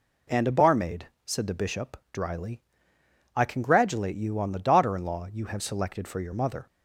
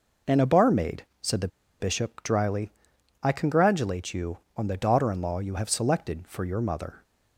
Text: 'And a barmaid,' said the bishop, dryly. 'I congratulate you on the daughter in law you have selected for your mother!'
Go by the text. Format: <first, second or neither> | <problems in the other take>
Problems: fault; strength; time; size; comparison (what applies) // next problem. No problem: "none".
first | pauses between "the" and "bishop"; slight; at 1.4 s; 0.31 s long